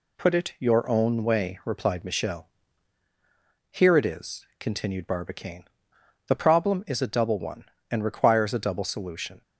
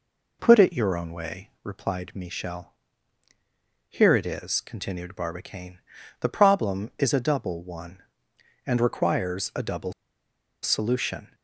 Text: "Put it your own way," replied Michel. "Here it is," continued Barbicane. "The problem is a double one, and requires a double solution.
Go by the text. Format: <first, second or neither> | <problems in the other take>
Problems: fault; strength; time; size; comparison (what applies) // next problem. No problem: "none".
first | pauses between "double" and "solution"; noticeable; at 9.9 s; 0.70 s long